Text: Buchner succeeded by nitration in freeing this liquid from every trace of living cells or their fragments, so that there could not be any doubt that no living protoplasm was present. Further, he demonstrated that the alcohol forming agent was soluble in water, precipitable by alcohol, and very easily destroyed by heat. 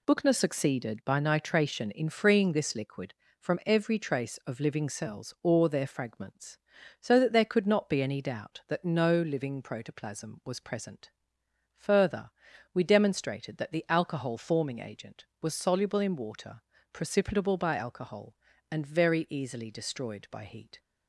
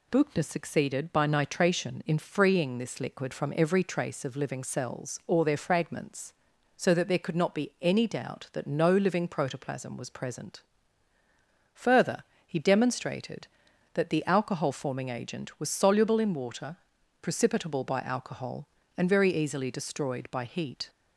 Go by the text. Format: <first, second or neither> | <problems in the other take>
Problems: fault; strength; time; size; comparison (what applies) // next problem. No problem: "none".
second | says "we" for "he"; at 12.7 s